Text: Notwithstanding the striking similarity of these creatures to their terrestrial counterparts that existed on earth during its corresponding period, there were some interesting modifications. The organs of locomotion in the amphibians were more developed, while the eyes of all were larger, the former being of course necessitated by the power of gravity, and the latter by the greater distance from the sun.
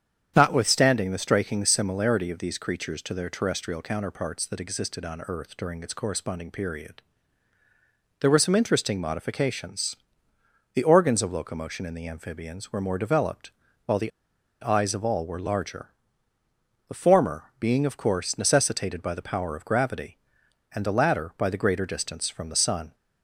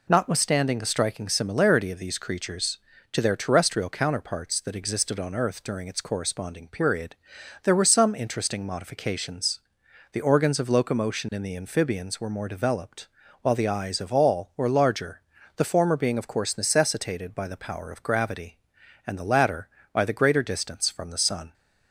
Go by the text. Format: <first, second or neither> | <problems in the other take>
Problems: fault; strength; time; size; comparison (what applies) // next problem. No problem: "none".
second | starts louder than the rest; strong; until 1.3 s; 8.5 dB // pauses between "the" and "eyes"; noticeable; at 14.1 s; 0.51 s long